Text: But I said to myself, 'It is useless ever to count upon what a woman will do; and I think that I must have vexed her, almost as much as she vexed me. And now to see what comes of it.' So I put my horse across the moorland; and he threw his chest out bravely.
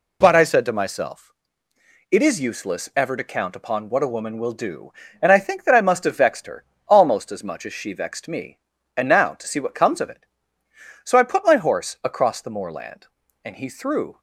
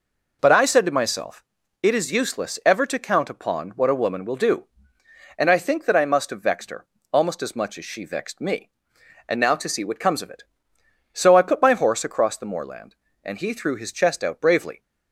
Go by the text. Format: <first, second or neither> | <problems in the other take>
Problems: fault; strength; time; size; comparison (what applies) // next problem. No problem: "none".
second | stops before "his chest out bravely"; at 14.1 s